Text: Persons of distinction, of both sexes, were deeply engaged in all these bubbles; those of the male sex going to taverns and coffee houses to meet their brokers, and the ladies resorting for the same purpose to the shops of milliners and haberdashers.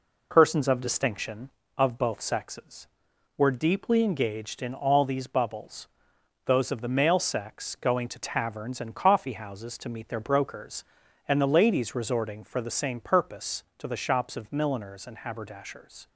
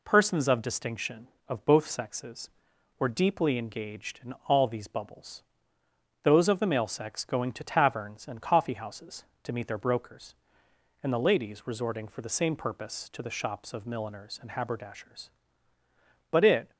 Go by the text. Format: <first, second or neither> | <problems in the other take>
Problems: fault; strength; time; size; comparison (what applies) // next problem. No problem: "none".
first | goes on to say "But it"; slight; from 16.3 s on; 0.40 s long